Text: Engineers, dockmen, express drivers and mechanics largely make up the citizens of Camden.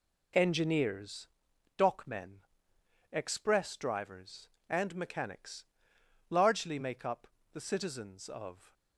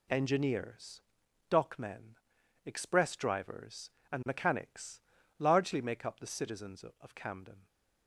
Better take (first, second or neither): second